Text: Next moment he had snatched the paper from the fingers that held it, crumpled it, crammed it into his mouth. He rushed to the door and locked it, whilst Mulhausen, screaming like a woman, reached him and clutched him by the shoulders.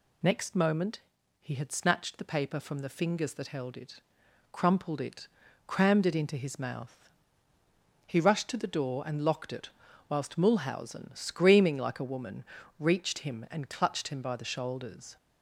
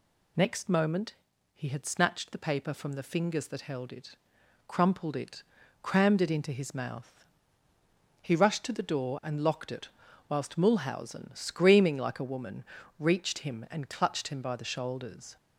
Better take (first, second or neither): neither